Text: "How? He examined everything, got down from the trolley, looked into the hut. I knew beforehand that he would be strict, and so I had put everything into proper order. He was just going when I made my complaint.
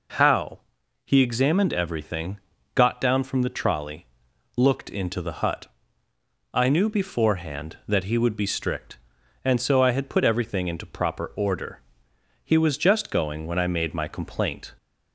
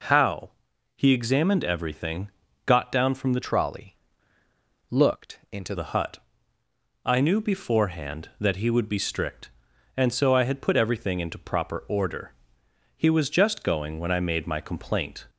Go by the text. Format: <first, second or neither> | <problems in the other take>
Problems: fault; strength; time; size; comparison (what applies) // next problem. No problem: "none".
first | changes voice from "trolley" to "into"; from 3.4 to 5.7 s; 2.3 s long